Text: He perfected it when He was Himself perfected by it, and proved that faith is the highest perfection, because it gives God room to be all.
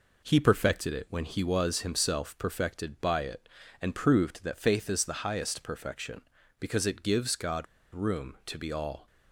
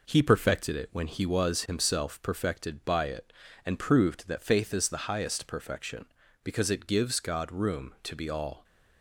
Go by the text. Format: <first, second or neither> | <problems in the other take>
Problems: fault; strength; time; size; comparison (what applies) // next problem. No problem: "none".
second | pauses between "God" and "room"; slight; at 7.6 s; 0.28 s long